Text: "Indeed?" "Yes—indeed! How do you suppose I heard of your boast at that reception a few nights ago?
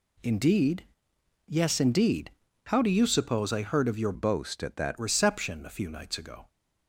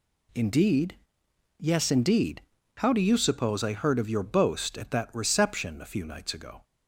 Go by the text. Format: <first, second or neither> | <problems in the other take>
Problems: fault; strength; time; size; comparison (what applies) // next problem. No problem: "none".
second | changes voice from "boast" to "that"; from 4.1 to 4.9 s; 0.8 s long